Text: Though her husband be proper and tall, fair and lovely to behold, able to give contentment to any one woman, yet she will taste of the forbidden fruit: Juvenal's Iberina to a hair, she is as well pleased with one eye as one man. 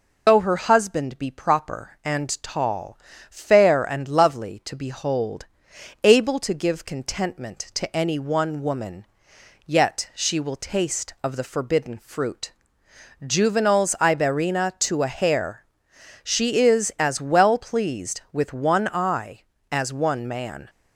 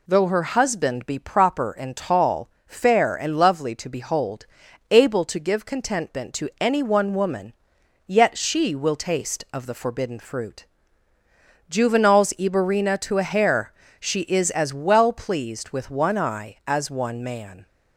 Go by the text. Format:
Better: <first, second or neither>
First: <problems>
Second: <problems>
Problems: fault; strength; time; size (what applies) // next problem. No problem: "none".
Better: second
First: loses the start of "Though"; at 0.2 s; 95 ms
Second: none